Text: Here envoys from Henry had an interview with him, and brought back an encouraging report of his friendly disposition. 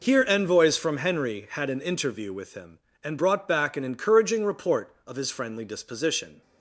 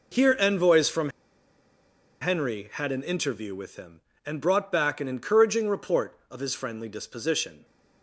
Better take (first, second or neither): first